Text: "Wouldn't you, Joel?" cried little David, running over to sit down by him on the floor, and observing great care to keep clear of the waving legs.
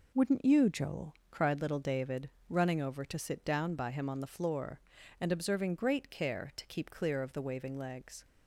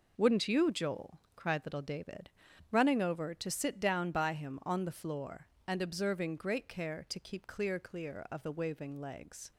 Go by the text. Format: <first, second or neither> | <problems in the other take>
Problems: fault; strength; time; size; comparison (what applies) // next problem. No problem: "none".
first | says "clear" twice; at 7.7 s